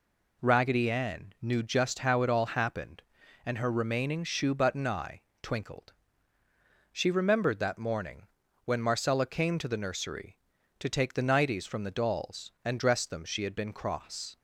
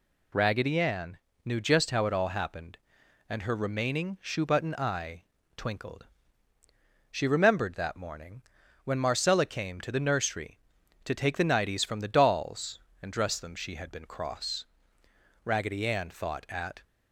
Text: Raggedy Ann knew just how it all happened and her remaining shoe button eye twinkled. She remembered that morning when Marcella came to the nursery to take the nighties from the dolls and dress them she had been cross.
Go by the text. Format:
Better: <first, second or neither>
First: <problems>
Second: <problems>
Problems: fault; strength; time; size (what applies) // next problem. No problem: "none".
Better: first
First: pauses between "eye" and "twinkled"; slight; at 5.2 s; 0.20 s long // pauses between "morning" and "when"; at 8.2 s; 0.38 s long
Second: pauses between "Ann" and "knew"; slight; at 1.1 s; 0.28 s long // pauses between "eye" and "twinkled"; slight; at 5.2 s; 0.32 s long // pauses between "morning" and "when"; at 8.4 s; 0.42 s long // goes on to say "Raggedy Ann thought at"; from 15.4 s on; 1.3 s long